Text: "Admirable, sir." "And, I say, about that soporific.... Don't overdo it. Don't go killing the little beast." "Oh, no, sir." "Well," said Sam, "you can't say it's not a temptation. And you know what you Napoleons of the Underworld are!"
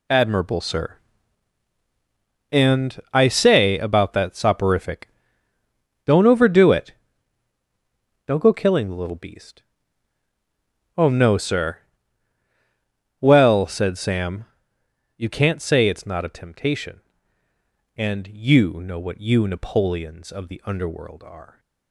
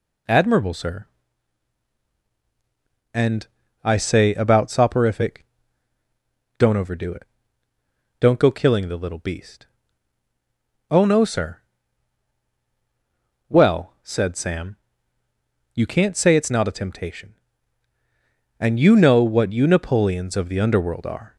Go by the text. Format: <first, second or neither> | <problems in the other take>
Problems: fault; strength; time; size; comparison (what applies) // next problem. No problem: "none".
first | skips "that"; at 4.6 s